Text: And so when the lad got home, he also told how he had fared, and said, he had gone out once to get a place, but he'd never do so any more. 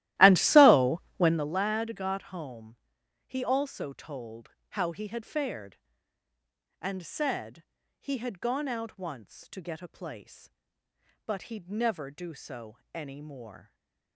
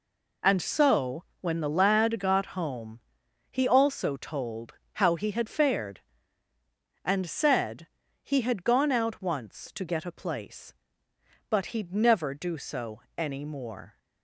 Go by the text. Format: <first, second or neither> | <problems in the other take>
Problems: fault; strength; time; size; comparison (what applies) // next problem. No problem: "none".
second | starts louder than the rest; strong; until 1.5 s; 15.5 dB // pauses between "so" and "when"; slight; at 1.0 s; 0.16 s long; slight in the second // pauses between "told" and "how"; slight; at 4.5 s; 0.20 s long; slight in the second // pauses between "so" and "any"; slight; at 12.7 s; 0.16 s long; slight in the second // stays silent after the last word; slight; from 13.6 s on; 0.5 s long